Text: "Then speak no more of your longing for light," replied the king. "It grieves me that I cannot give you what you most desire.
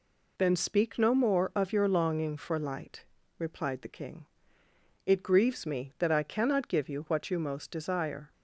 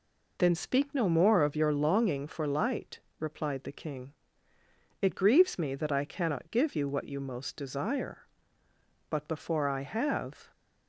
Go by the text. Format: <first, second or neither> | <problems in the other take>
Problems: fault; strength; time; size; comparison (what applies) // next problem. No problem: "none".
first | goes on to say "But before I have"; from 9.0 s on; 1.4 s long